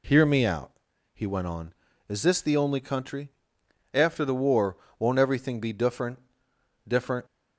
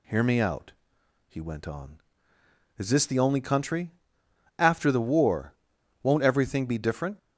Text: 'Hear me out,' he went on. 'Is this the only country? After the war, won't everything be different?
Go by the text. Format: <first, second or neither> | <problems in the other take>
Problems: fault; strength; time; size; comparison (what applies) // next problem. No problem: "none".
second | says "different" twice; at 6.8 s